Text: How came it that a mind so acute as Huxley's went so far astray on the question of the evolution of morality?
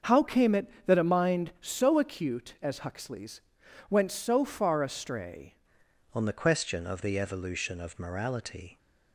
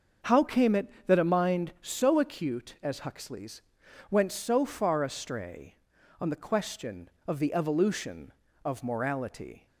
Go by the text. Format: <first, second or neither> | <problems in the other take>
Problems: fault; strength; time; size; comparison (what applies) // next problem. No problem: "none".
second | starts louder than the rest; until 1.2 s; 6.5 dB; also in the second // pauses between "Huxley's" and "went"; noticeable; at 3.4 s; 0.48 s long; noticeable in the second // changes voice at "on"; from 6.1 s on; 2.6 s long